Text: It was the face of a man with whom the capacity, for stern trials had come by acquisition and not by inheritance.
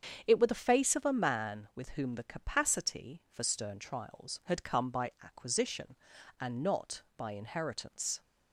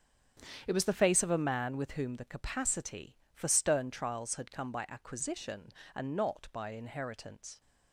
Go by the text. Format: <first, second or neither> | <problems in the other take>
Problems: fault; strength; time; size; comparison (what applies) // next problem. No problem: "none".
second | starts louder than the rest; strong; until 1.2 s; 7.5 dB; strong in the second // says "were" for "was"; at 0.3 s